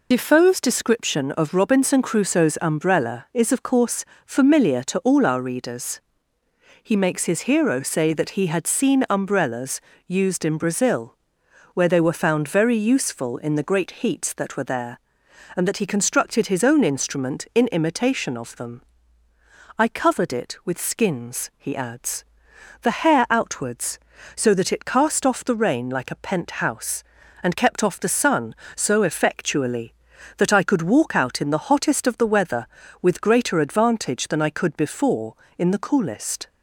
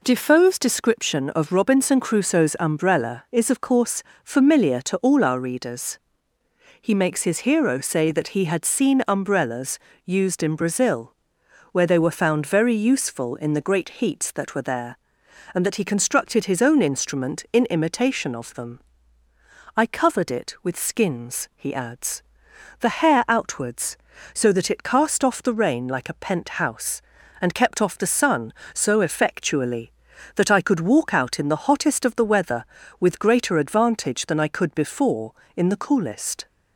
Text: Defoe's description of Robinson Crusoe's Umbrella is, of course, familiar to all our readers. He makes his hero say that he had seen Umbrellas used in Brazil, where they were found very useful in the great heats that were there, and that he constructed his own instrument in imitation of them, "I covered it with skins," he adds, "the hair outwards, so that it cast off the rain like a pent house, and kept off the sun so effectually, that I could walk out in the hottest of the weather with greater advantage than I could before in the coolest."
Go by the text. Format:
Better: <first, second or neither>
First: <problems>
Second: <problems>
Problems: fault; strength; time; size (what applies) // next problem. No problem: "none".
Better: second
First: loses the start of "Defoe's"; at 0.1 s; 60 ms // pauses between "Umbrellas" and "used"; slight; at 9.8 s; 0.26 s long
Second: pauses between "Umbrellas" and "used"; slight; at 9.7 s; 0.26 s long